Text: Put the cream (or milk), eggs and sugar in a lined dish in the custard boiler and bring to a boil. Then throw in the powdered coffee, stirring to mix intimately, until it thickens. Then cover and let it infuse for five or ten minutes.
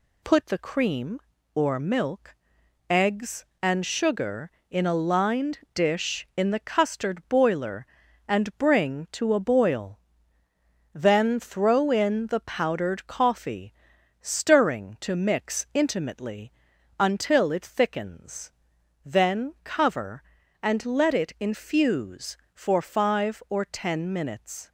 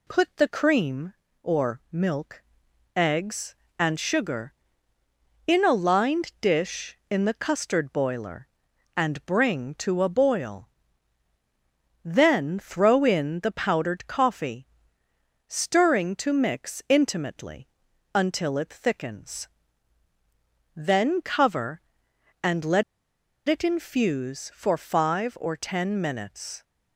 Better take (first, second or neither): first